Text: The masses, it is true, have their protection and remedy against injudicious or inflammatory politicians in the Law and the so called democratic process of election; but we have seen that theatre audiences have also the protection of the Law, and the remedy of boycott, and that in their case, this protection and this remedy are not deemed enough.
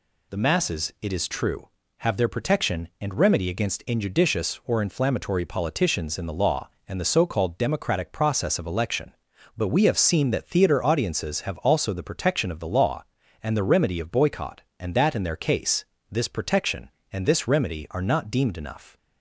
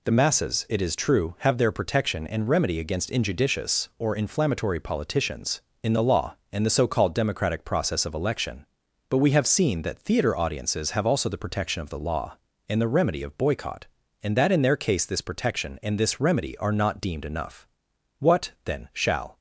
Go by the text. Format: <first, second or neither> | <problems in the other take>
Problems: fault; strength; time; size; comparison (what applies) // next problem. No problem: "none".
first | goes on to say "What then shall"; noticeable; from 18.1 s on; 1.2 s long